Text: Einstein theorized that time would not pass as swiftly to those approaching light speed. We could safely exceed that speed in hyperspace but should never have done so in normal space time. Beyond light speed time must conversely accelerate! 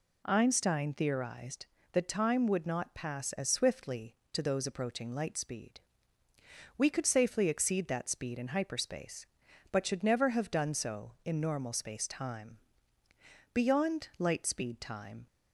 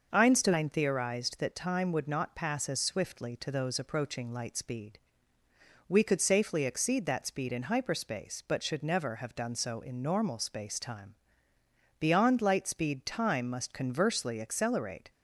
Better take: second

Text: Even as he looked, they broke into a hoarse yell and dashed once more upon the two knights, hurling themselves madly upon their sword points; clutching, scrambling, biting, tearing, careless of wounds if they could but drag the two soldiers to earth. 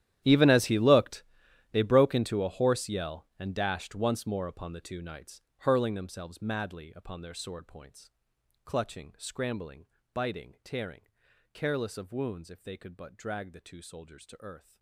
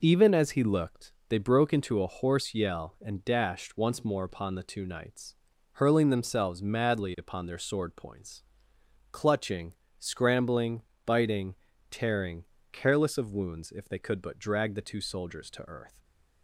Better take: second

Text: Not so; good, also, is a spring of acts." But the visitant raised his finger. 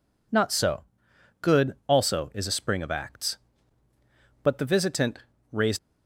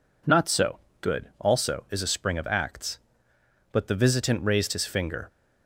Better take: second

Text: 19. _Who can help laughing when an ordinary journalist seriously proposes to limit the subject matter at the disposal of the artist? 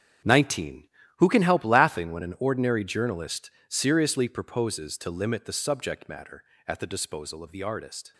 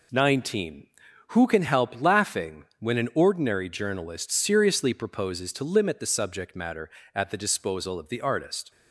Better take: second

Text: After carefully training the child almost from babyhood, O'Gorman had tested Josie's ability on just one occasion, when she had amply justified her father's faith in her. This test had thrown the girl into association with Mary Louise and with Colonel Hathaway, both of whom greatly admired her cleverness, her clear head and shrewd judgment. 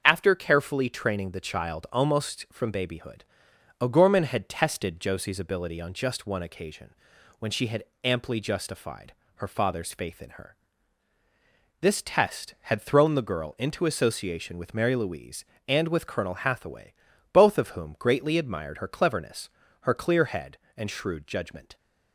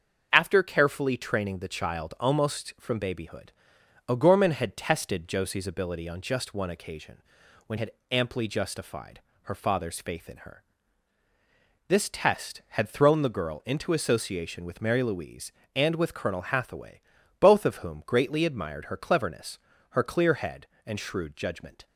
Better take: first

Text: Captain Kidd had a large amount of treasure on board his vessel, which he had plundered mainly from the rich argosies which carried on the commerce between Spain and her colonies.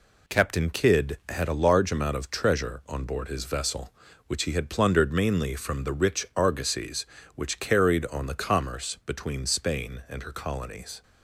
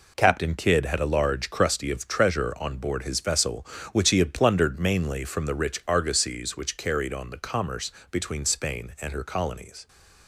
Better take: first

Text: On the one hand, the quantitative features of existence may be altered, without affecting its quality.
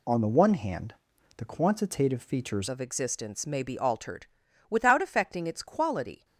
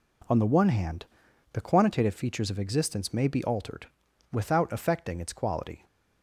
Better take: second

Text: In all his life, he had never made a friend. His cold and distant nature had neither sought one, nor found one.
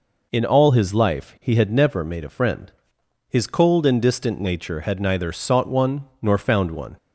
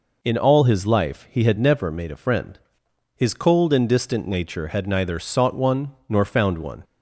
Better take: neither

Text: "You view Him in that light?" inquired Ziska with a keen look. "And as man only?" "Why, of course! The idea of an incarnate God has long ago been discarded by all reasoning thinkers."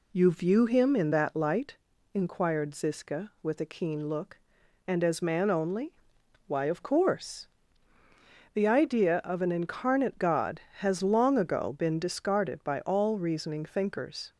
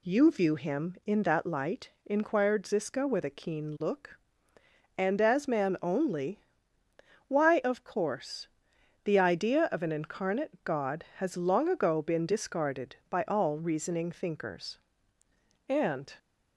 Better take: first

